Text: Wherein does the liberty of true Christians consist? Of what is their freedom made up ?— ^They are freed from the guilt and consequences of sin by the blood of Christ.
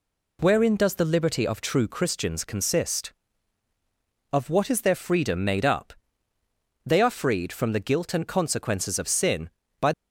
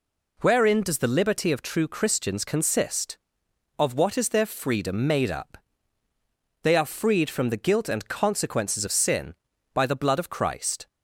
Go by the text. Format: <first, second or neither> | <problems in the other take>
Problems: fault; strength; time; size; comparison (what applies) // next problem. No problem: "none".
second | stops before "the blood of Christ"; at 9.9 s